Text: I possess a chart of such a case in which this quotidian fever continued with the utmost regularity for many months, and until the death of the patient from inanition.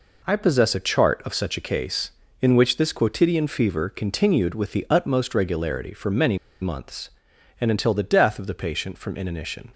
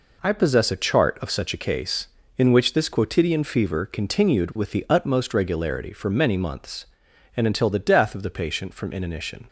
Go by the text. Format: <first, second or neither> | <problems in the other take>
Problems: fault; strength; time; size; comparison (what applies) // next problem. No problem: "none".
second | pauses between "many" and "months"; slight; at 6.3 s; 0.23 s long